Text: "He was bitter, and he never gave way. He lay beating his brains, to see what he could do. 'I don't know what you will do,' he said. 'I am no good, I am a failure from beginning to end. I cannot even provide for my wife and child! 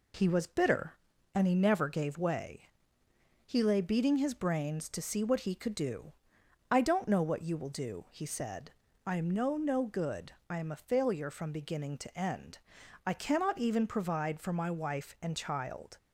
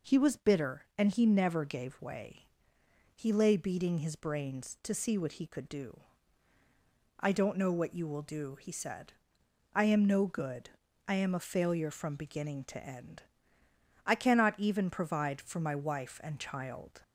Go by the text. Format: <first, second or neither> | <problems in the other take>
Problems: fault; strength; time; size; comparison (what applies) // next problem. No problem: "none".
second | says "no" twice; at 9.5 s